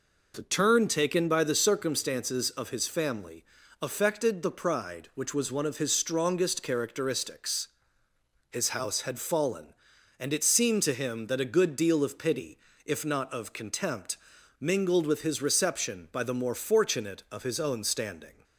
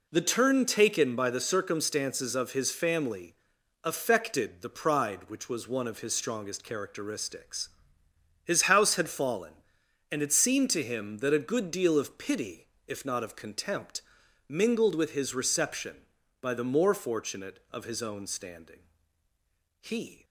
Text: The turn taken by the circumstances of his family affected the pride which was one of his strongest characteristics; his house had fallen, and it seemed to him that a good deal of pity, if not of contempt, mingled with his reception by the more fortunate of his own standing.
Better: first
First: pauses between "family" and "affected"; slight; at 3.4 s; 0.36 s long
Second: pauses between "family" and "affected"; noticeable; at 3.3 s; 0.50 s long // goes on to say "He"; slight; from 19.8 s on; 0.42 s long

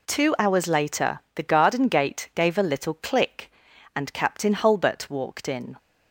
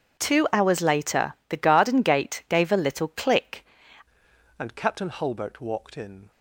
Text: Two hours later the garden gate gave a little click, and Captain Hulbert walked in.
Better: first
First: pauses between "later" and "the"; slight; at 1.1 s; 0.16 s long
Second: pauses between "later" and "the"; slight; at 1.3 s; 0.16 s long // changes voice at "and"; from 4.5 s on; 1.8 s long

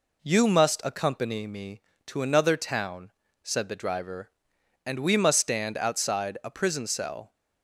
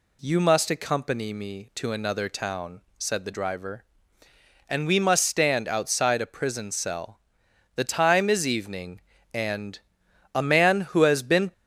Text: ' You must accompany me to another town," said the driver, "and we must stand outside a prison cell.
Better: first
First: none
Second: goes on to say "The time is evening and a man who has been"; strong; from 7.7 s on; 3.7 s long

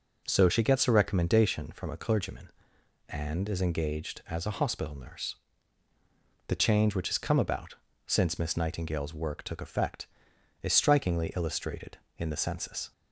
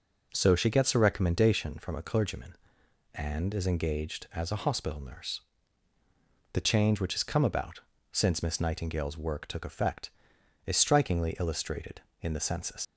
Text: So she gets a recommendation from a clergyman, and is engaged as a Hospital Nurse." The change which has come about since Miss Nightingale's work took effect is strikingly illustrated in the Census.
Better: first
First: pauses between "about" and "since"; slight; at 7.7 s; 0.30 s long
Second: pauses between "about" and "since"; slight; at 7.8 s; 0.30 s long // leaves "Census" unfinished; at 12.8 s; 105 ms

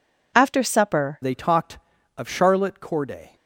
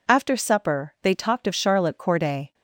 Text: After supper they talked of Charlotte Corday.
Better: second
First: changes voice at "they"; from 1.2 s on; 2.1 s long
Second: none

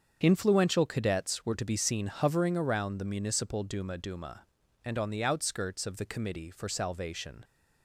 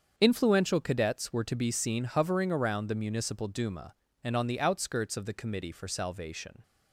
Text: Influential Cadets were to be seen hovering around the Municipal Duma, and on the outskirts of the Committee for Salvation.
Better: second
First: starts louder than the rest; strong; until 1.2 s; 7 dB // says "Duma" twice; at 3.9 s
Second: starts louder than the rest; until 1.1 s; 7 dB

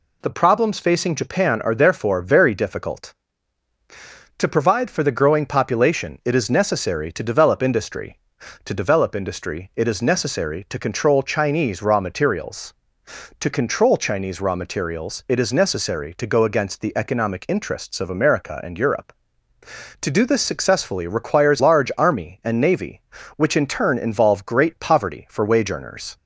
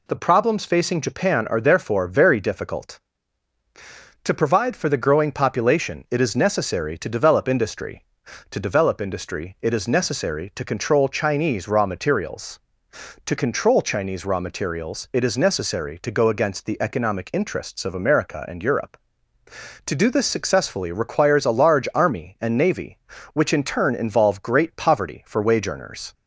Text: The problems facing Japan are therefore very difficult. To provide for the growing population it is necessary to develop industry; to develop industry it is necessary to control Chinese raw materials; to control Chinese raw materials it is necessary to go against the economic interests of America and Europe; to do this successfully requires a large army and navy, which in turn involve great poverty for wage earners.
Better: second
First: skips "a"; at 21.6 s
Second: none

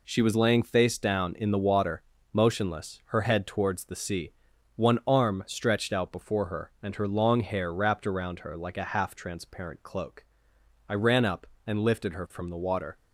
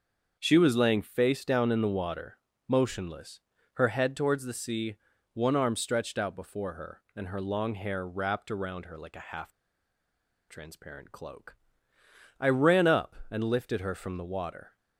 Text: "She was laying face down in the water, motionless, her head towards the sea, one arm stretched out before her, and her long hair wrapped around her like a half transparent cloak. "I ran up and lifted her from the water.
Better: first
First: none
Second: starts louder than the rest; until 1.4 s; 6.5 dB // pauses between "half" and "transparent"; at 9.4 s; 0.98 s long

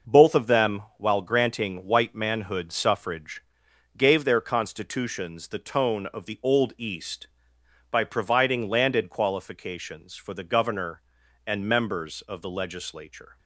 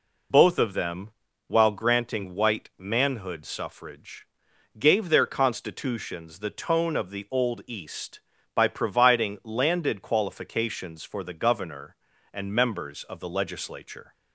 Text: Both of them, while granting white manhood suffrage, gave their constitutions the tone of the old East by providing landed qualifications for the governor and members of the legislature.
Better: first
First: none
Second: loses the start of "Both"; at 0.3 s; 65 ms

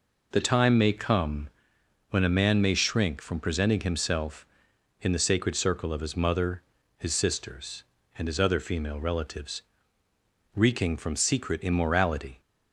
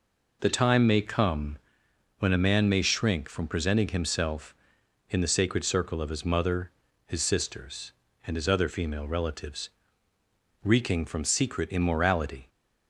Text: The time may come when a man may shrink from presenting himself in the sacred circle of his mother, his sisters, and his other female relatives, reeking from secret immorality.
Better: neither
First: pauses between "come" and "when"; noticeable; at 1.4 s; 0.62 s long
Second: pauses between "come" and "when"; noticeable; at 1.5 s; 0.62 s long

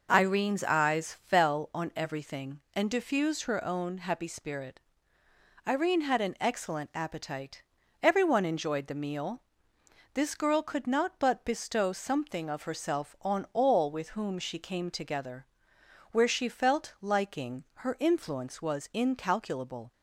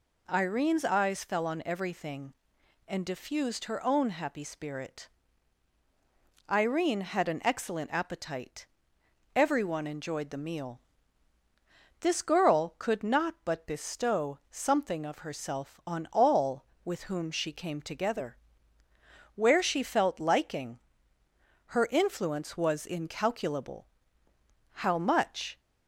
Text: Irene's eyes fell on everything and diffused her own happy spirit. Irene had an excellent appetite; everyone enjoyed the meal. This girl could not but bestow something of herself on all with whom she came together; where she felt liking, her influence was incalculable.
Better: first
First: none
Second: goes on to say "How much"; noticeable; from 24.7 s on; 0.88 s long

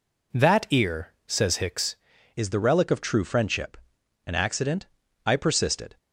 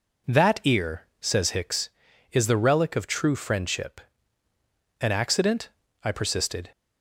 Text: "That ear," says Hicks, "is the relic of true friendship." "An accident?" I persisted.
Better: second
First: changes voice at "is"; from 2.3 s on; 3.6 s long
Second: none

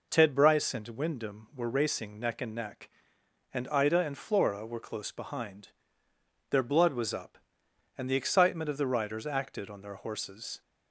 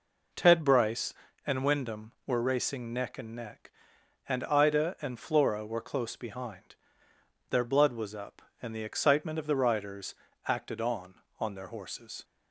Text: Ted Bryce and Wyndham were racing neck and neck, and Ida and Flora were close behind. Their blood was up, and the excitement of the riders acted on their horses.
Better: first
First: none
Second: pauses between "riders" and "acted"; slight; at 10.1 s; 0.34 s long // says "on" twice; at 11.3 s

